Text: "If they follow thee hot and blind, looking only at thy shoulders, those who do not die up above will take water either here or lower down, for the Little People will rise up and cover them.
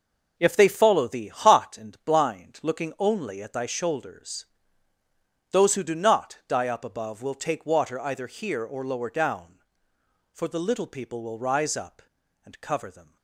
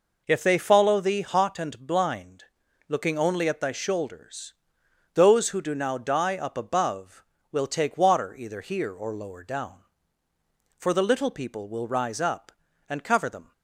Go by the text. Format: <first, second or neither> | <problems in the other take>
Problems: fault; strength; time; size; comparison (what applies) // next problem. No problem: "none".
first | says "now" for "not"; at 5.7 s